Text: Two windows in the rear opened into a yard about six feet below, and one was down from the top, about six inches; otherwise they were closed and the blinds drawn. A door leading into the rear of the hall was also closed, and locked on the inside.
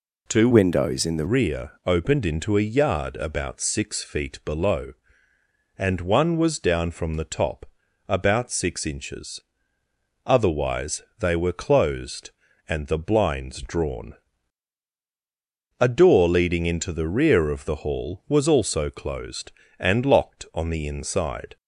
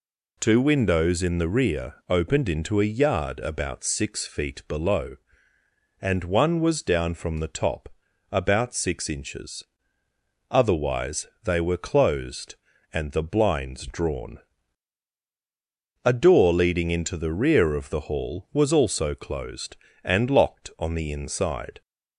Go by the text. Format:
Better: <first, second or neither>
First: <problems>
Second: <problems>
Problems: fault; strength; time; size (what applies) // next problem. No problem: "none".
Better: second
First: changes voice from "windows" to "the"; from 0.5 to 1.2 s; 0.7 s long // pauses between "otherwise" and "they"; slight; at 11.0 s; 0.16 s long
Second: pauses between "otherwise" and "they"; slight; at 11.2 s; 0.16 s long